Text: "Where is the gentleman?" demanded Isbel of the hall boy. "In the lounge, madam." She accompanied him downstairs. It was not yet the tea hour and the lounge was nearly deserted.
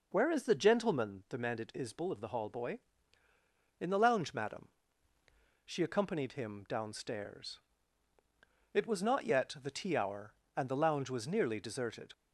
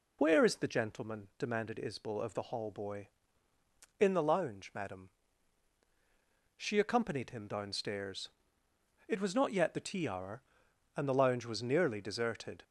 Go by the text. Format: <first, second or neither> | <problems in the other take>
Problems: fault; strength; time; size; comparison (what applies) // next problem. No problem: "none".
first | loses the start of "Where"; at 0.1 s; 45 ms